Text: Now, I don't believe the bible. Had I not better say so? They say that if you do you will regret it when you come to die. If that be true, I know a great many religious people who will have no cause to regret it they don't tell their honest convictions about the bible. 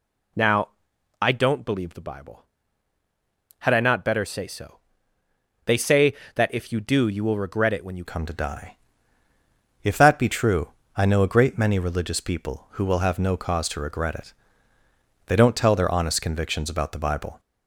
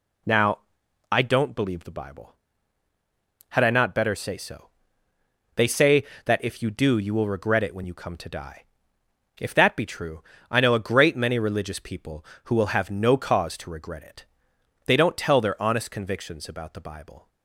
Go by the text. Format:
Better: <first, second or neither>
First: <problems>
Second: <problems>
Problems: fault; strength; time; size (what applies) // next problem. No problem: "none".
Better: second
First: changes voice at "come"; from 8.0 s on; 9.3 s long // pauses between "it" and "they"; noticeable; at 14.3 s; 0.94 s long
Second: pauses between "it" and "they"; noticeable; at 14.2 s; 0.60 s long